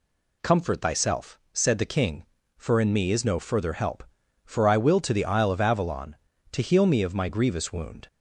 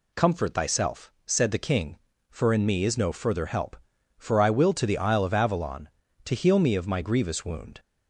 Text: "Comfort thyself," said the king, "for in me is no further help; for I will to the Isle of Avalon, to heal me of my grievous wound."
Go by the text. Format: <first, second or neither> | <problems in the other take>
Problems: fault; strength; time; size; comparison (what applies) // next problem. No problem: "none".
neither | none